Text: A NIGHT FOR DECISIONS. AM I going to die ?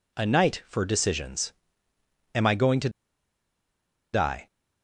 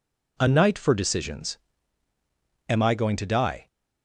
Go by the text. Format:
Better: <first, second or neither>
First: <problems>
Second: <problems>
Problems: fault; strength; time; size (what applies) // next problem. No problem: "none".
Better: second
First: pauses between "to" and "die"; at 2.8 s; 1.2 s long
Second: none